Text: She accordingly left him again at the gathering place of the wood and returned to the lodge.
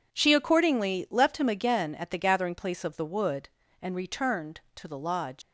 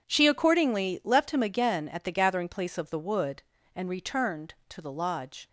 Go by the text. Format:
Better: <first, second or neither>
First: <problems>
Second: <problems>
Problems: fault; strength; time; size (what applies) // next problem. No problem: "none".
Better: second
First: leaves "lodge" unfinished; at 5.4 s; 125 ms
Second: none